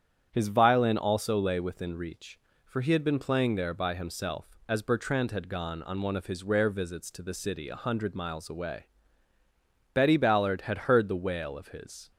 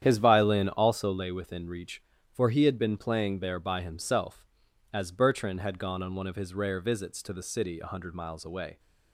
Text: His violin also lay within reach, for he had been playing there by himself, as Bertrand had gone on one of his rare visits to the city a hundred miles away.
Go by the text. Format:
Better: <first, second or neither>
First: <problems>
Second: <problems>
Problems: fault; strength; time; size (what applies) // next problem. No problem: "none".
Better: second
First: starts louder than the rest; strong; until 1.3 s; 9 dB // goes on to say "Betty Ballard had heard the wail of his"; strong; from 9.9 s on; 2.1 s long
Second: starts louder than the rest; strong; until 1.0 s; 9.5 dB